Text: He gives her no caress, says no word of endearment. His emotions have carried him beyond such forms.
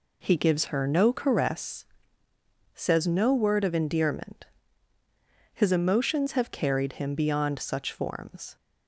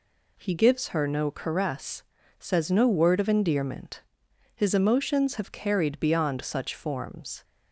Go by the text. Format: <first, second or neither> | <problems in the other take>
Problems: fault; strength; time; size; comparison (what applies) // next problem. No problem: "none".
first | skips "him"; at 5.9 s